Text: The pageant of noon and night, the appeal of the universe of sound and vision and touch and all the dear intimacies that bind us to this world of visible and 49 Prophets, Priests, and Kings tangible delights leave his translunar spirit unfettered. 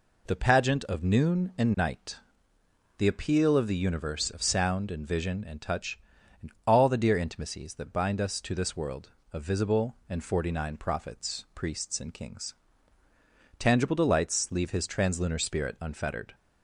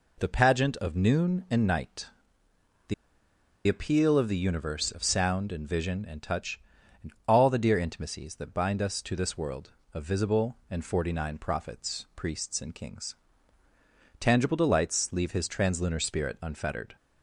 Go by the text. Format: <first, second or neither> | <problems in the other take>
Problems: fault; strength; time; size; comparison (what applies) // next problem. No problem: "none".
first | pauses between "the" and "appeal"; noticeable; at 2.9 s; 0.73 s long // pauses between "and" and "all"; slight; at 7.1 s; 0.16 s long; slight in the first // pauses between "Kings" and "tangible"; at 13.1 s; 1.0 s long; also in the first